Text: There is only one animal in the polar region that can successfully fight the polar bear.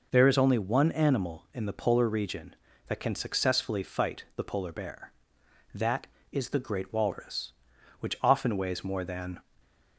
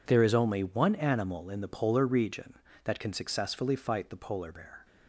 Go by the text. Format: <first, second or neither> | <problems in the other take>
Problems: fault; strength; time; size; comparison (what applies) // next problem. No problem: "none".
second | goes on to say "That is the great walrus which often weighs more than"; strong; from 5.7 s on; 3.6 s long